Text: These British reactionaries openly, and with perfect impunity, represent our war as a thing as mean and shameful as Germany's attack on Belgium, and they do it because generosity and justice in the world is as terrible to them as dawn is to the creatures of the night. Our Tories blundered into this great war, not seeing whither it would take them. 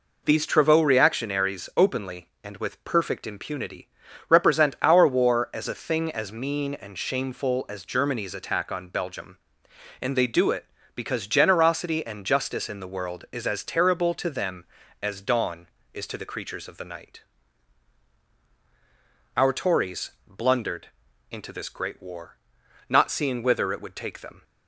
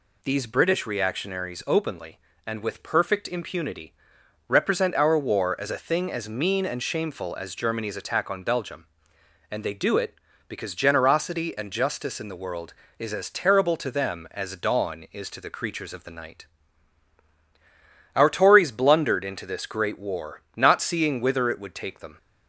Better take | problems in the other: second | says "Travaux" for "British"; at 0.4 s // pauses between "Tories" and "blundered"; slight; at 20.1 s; 0.16 s long // pauses between "blundered" and "into"; at 20.8 s; 0.44 s long

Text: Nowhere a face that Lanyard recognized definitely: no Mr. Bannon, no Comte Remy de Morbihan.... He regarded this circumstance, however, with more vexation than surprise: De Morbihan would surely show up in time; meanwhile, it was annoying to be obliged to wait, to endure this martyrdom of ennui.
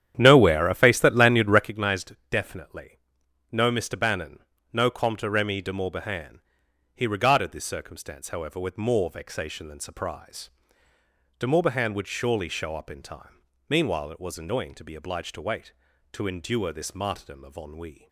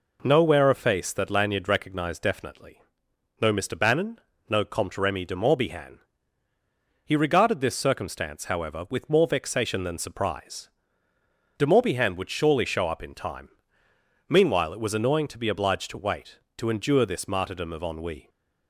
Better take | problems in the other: second | starts louder than the rest; strong; until 1.7 s; 10 dB

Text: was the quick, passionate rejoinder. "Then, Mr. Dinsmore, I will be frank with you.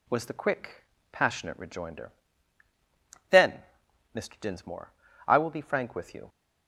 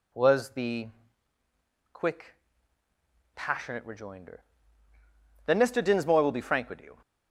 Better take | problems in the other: first | pauses between "the" and "quick"; at 0.8 s; 1.0 s long // skips "I"; at 6.2 s

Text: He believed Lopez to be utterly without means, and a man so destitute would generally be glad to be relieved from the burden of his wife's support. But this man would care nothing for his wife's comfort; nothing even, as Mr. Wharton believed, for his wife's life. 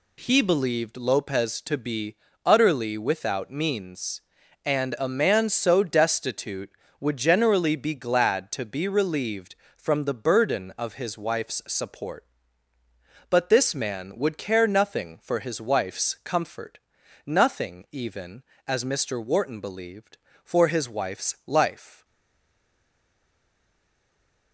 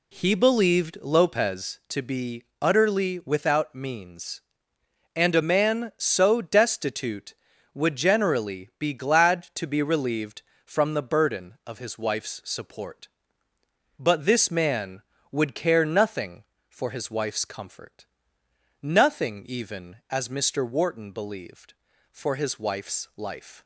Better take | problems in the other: second | pauses between "be" and "utterly"; slight; at 2.1 s; 0.28 s long; slight in the second // stays silent after the last word; strong; from 22.0 s on; 2.5 s long

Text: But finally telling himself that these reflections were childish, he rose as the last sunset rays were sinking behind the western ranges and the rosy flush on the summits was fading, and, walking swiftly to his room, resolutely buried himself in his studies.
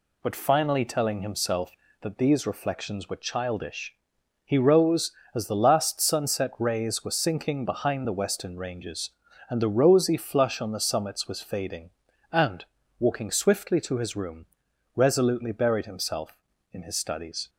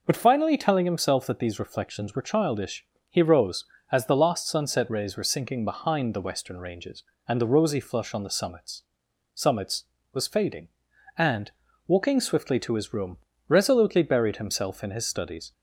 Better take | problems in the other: first | says "summits" twice; at 9.3 s

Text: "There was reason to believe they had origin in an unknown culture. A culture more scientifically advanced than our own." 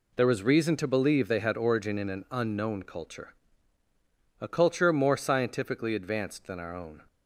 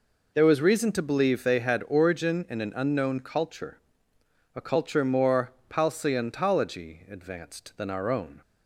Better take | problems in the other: first | says "palseontology" for "scientifically"; at 5.6 s

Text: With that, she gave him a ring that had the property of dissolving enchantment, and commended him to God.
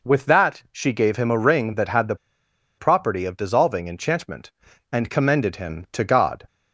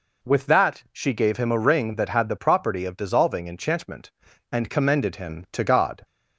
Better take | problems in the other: second | pauses between "the" and "property"; noticeable; at 2.1 s; 0.63 s long

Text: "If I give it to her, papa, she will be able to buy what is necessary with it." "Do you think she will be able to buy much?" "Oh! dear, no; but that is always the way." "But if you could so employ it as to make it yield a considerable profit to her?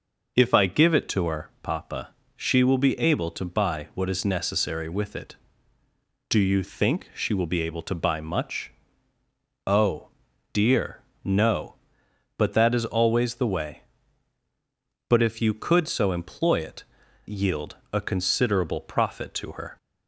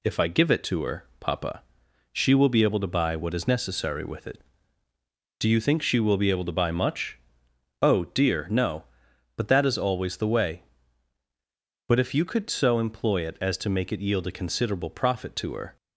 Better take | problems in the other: second | skips "as to make it"; at 17.0 s // pauses between "yield" and "a"; slight; at 17.7 s; 0.16 s long

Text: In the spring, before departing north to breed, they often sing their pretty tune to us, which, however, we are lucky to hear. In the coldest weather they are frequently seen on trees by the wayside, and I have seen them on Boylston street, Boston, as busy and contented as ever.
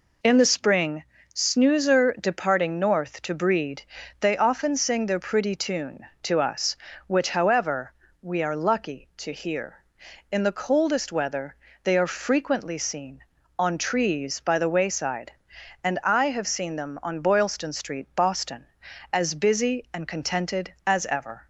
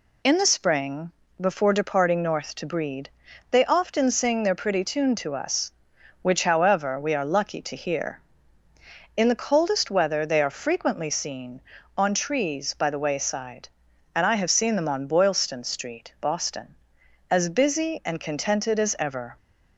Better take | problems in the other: second | says "snoozer" for "before"; at 1.3 s // pauses between "weather" and "they"; slight; at 11.5 s; 0.30 s long

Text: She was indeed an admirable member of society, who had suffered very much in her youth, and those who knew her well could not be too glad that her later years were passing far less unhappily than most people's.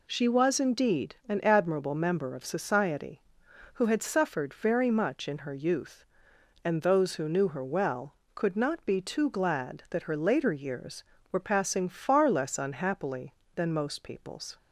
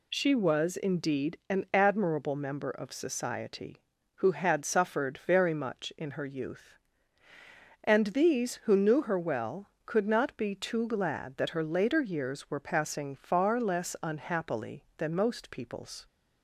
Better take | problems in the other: first | says "these" for "those"; at 8.0 s

